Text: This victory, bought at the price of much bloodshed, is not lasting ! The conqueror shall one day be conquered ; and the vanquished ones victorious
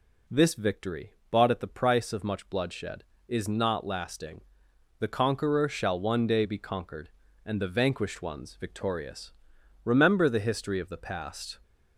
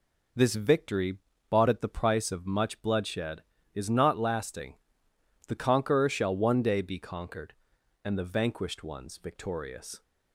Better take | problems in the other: second | goes on to say "Remember the history of the past"; strong; from 9.8 s on; 1.7 s long

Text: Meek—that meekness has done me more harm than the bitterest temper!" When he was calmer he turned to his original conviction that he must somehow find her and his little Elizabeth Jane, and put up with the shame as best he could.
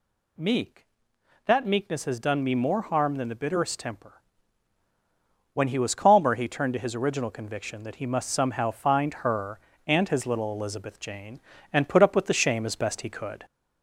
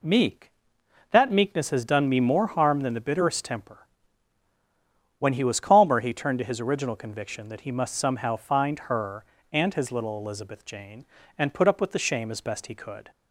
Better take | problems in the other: second | gets louder; slight; throughout; 2 dB

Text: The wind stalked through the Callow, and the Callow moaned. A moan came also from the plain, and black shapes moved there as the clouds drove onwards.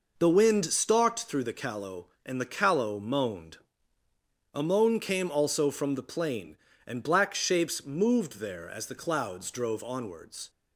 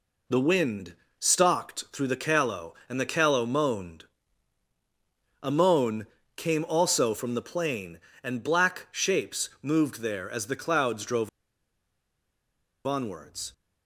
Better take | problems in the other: first | pauses between "wind" and "stalked"; slight; at 0.9 s; 0.26 s long // pauses between "moan" and "came"; slight; at 6.0 s; 0.30 s long // pauses between "drove" and "onwards"; strong; at 11.2 s; 1.5 s long

